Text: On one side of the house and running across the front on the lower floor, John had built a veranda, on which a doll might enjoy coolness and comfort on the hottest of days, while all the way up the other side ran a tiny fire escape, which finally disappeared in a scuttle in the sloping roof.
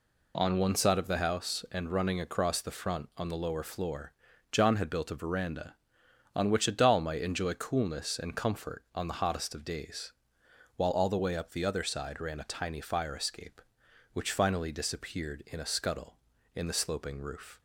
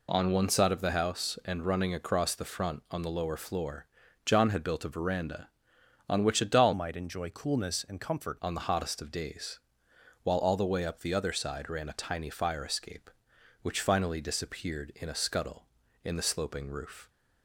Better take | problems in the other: first | changes voice from "might" to "comfort"; from 6.7 to 8.3 s; 1.6 s long

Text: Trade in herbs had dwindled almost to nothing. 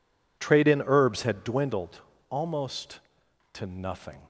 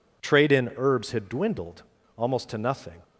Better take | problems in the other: neither | pauses between "dwindled" and "almost"; slight; the same in both

